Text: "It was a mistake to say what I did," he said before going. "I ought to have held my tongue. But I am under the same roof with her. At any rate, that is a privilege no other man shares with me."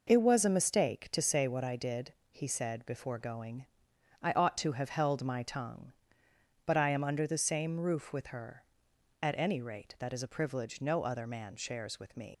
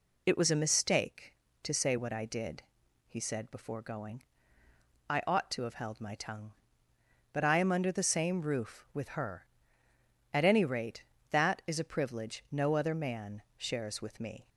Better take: second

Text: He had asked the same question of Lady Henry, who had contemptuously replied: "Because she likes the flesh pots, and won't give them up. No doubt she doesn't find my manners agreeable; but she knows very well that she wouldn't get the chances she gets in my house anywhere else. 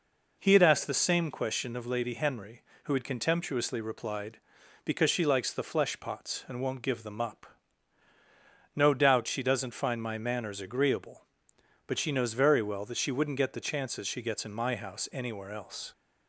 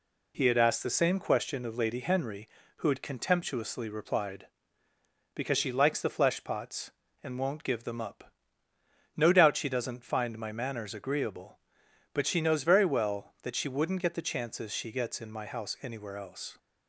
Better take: neither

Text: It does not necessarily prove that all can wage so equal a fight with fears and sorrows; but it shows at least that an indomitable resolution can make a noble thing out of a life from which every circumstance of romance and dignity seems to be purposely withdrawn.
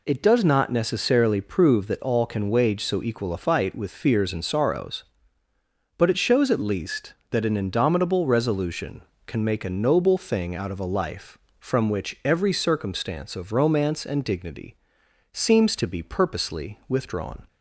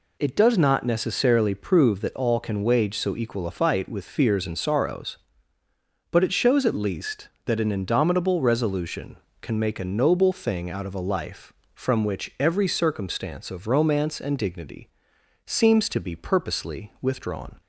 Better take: neither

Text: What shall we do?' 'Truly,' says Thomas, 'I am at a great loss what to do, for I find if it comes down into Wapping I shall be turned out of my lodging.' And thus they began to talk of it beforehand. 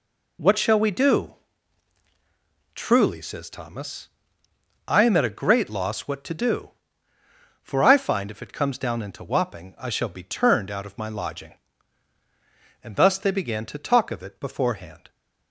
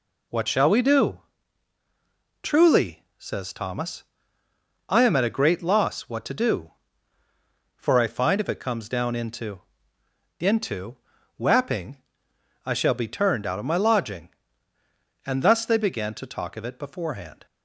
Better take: first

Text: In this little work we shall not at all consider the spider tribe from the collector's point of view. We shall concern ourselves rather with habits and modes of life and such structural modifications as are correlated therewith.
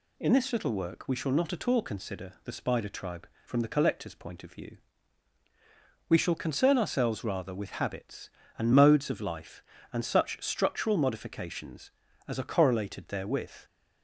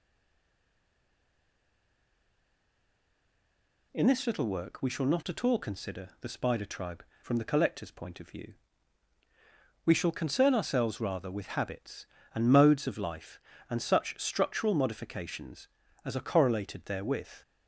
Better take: first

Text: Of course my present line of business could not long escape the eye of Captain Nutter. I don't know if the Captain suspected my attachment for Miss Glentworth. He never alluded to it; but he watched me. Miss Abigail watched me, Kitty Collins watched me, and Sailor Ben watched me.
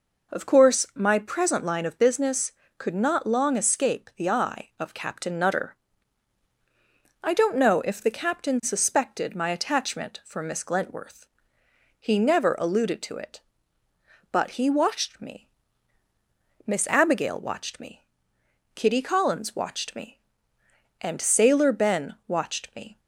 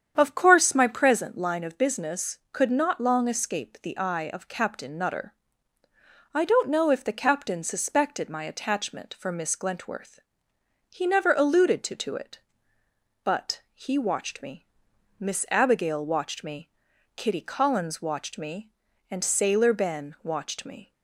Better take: first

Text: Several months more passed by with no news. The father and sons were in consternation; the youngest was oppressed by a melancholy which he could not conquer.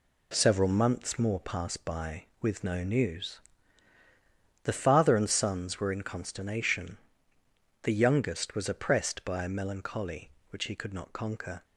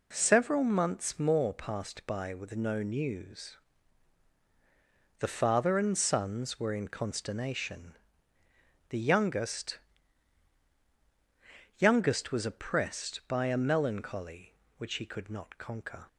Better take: first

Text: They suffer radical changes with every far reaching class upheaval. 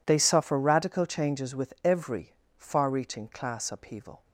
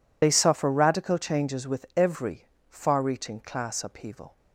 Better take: first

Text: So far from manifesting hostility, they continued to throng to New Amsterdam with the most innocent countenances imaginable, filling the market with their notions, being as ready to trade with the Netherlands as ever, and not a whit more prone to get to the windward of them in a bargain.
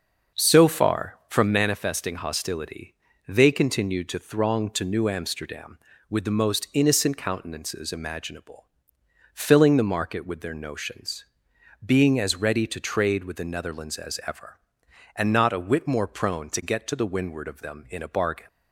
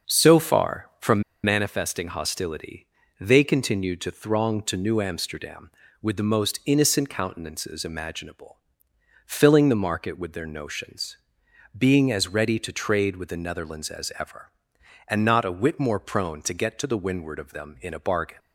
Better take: first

